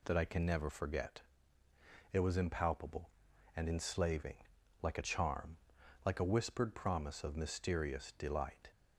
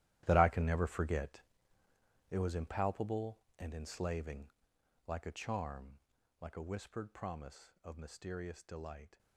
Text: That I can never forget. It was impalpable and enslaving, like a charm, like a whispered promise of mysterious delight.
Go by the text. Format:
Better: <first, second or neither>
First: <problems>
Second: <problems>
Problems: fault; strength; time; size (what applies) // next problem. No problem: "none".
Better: first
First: none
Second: gets quieter; strong; throughout; 15 dB